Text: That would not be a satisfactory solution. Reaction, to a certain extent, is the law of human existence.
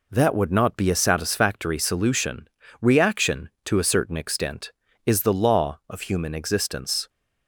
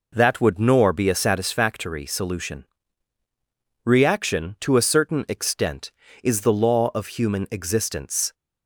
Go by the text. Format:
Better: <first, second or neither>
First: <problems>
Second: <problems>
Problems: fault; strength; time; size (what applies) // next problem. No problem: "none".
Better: first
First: none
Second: says "nor" for "not"; at 0.5 s